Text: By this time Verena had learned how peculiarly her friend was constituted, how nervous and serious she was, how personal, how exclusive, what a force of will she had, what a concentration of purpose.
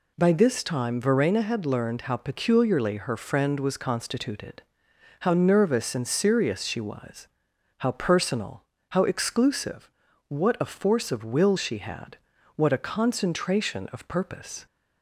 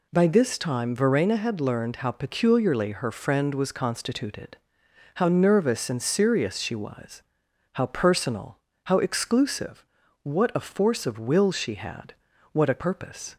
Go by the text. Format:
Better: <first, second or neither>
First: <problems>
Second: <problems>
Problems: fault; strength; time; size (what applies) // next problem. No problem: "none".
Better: first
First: none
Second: skips "concentration of"; at 12.8 s